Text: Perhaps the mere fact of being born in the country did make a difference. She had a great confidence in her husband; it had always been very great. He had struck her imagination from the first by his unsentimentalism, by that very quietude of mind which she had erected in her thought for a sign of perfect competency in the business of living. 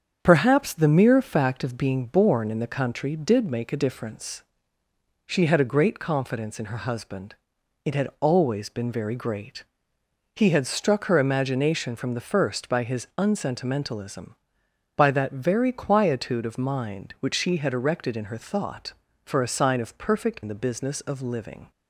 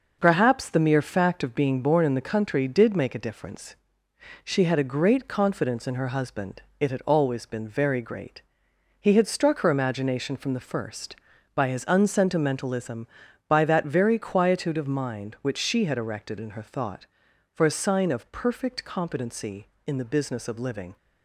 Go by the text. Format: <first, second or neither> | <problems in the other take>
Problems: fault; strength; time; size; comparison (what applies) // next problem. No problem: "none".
second | starts louder than the rest; strong; until 1.2 s; 7.5 dB // skips "competency"; at 20.4 s